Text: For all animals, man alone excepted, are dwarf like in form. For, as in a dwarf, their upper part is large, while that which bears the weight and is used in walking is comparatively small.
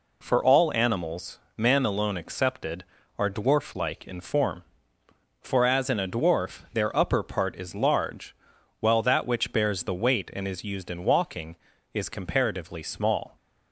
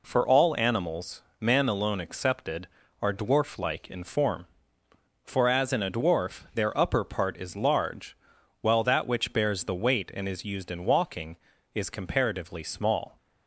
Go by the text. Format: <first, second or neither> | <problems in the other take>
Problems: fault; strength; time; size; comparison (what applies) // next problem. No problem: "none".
neither | none